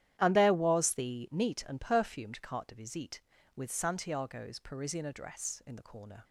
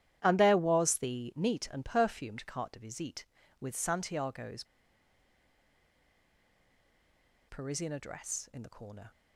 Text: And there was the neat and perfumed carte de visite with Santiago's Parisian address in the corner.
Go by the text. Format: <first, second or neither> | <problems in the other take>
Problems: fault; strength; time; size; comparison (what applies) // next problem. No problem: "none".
first | starts louder than the rest; strong; until 1.2 s; 11.5 dB; strong in the first // pauses between "Santiago's" and "Parisian"; strong; at 4.6 s; 2.8 s long